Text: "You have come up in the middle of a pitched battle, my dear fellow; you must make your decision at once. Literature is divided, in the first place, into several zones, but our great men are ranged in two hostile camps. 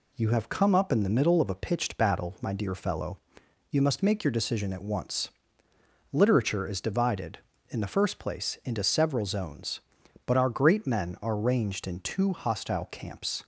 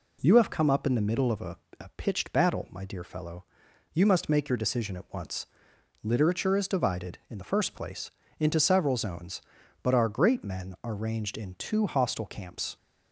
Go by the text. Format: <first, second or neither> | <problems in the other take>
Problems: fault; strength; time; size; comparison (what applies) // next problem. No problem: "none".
first | says "a" twice; at 1.7 s